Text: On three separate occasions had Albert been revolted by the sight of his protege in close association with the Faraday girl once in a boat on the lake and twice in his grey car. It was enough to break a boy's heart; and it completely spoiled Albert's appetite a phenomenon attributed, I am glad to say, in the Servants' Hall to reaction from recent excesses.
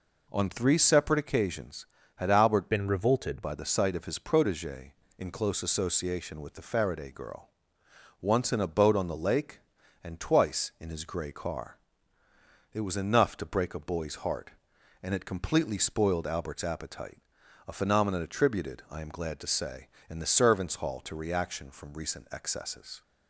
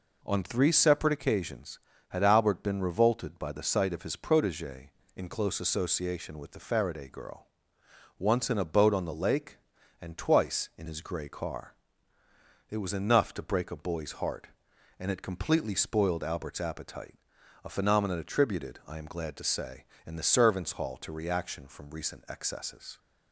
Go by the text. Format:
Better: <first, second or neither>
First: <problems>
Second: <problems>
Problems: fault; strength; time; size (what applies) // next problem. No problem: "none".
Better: second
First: changes voice from "been" to "revolted"; from 2.7 to 3.4 s; 0.7 s long // pauses between "girl" and "once"; noticeable; at 7.4 s; 0.72 s long // pauses between "appetite" and "a"; noticeable; at 17.1 s; 0.48 s long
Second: pauses between "girl" and "once"; noticeable; at 7.4 s; 0.72 s long // pauses between "appetite" and "a"; noticeable; at 17.1 s; 0.48 s long